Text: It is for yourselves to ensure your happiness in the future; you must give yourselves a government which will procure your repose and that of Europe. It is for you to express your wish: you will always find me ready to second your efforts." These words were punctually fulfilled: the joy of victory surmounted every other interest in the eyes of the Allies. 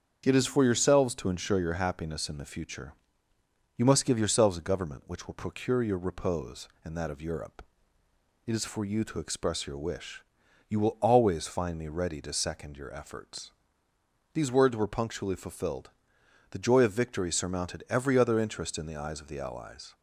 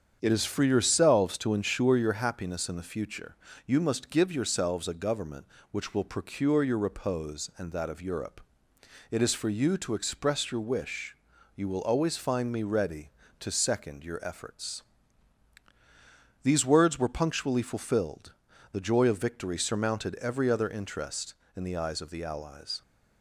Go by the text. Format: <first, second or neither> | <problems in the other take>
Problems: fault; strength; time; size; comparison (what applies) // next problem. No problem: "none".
neither | starts louder than the rest; strong; the same in both